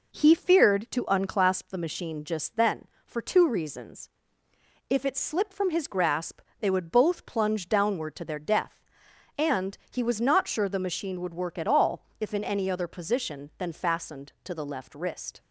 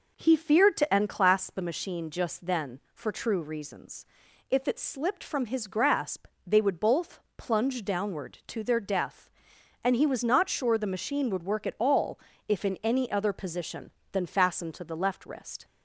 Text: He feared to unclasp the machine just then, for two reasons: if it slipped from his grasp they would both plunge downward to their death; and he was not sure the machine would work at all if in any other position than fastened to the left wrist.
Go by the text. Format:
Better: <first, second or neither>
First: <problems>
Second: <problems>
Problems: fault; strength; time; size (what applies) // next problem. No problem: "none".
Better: first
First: pauses between "grasp" and "they"; slight; at 6.4 s; 0.18 s long // pauses between "all" and "if"; slight; at 12.0 s; 0.16 s long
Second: says "true" for "two"; at 3.1 s // pauses between "grasp" and "they"; slight; at 6.2 s; 0.18 s long // pauses between "both" and "plunge"; slight; at 7.1 s; 0.20 s long // pauses between "all" and "if"; slight; at 12.1 s; 0.28 s long